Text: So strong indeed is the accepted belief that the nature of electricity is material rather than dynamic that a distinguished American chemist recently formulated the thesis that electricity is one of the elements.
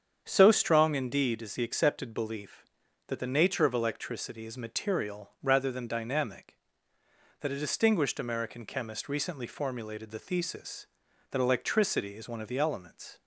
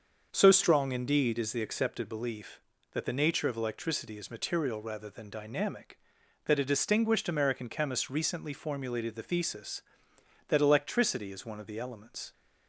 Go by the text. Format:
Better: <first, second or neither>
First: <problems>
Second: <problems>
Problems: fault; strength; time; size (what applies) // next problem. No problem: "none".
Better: neither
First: starts louder than the rest; strong; until 1.2 s; 7.5 dB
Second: starts louder than the rest; until 1.3 s; 6.5 dB